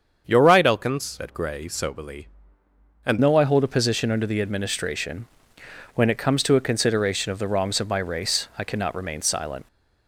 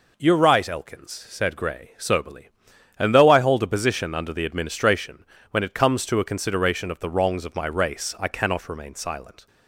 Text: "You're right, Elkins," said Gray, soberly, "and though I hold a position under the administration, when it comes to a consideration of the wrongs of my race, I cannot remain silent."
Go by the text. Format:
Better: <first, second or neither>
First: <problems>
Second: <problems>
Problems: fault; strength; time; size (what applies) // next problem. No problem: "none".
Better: second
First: starts louder than the rest; strong; until 1.2 s; 7 dB // changes voice at "though"; from 3.2 s on; 6.4 s long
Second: none